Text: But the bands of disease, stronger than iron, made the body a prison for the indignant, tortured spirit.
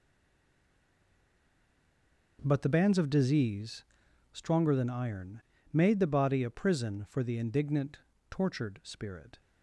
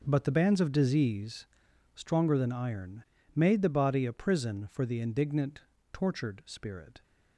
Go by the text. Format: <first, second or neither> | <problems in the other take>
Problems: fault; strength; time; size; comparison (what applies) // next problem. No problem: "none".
second | stays silent before the first word; until 2.3 s; 2.3 s long